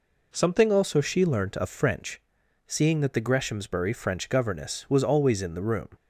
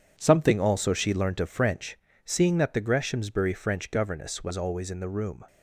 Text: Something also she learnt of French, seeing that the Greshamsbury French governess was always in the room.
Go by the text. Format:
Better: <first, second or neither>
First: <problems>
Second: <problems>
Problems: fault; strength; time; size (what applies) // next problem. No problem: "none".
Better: first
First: none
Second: gets quieter; strong; throughout; 9 dB